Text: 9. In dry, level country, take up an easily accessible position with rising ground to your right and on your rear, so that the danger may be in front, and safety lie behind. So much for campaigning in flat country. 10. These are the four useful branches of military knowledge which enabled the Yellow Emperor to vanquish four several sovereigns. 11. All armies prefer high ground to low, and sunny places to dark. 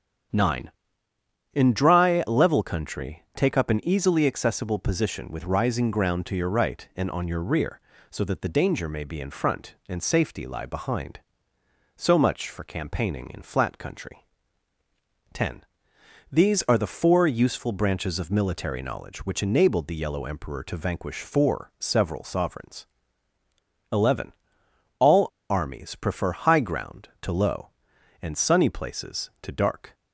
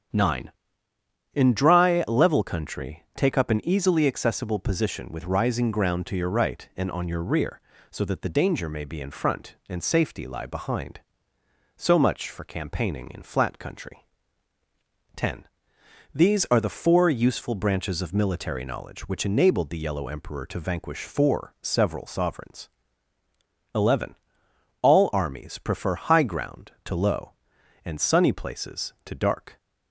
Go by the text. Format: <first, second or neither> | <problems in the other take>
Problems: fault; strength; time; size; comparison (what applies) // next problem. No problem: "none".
second | starts louder than the rest; strong; until 2.1 s; 8 dB; strong in the second // pauses between "All" and "armies"; slight; at 25.2 s; 0.23 s long